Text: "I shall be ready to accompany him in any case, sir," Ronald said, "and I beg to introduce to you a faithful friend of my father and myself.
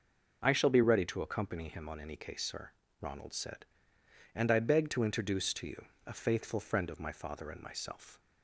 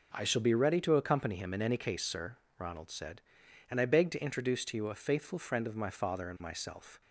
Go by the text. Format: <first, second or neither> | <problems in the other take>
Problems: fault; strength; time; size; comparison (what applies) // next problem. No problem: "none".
second | says "on" for "in"; at 1.8 s // pauses between "you" and "a"; slight; at 5.8 s; 0.20 s long